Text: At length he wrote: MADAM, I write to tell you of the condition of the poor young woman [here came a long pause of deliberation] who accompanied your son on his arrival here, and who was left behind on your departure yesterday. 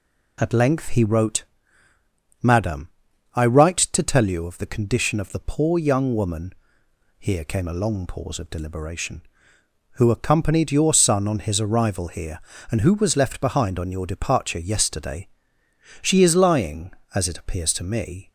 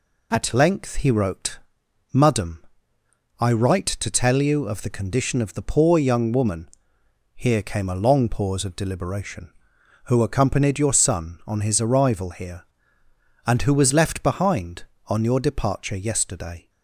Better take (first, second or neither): second